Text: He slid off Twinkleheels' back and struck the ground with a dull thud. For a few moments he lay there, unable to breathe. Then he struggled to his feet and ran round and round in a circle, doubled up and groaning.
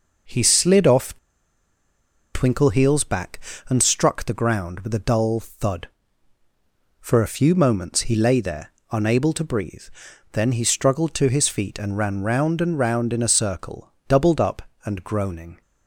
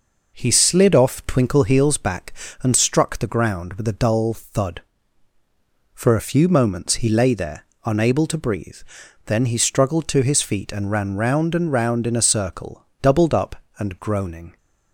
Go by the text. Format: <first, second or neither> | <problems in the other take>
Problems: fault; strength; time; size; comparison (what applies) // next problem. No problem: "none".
second | pauses between "off" and "Twinkleheels"; at 1.1 s; 1.1 s long